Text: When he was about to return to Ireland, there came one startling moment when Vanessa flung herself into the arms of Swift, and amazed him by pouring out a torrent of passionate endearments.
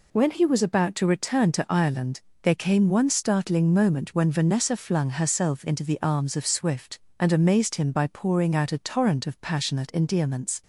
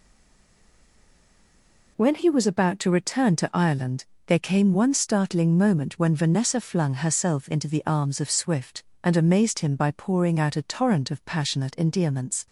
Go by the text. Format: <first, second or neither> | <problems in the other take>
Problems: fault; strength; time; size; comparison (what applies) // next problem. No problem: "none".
first | stays silent before the first word; noticeable; until 1.9 s; 1.9 s long